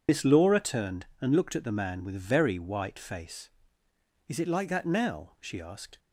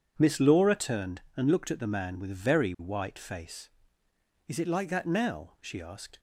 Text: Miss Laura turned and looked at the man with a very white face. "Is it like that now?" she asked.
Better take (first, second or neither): second